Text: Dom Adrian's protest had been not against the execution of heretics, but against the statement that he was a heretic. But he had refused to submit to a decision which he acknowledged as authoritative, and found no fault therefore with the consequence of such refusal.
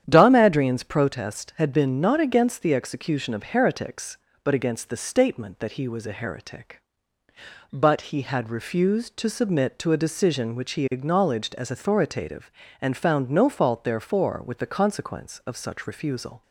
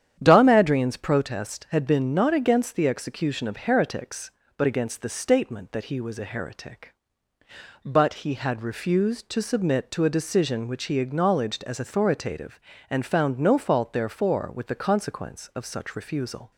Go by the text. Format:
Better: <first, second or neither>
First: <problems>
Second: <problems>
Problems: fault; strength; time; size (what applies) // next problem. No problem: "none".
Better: neither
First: starts louder than the rest; strong; until 1.0 s; 9.5 dB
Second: starts louder than the rest; strong; until 1.2 s; 9.5 dB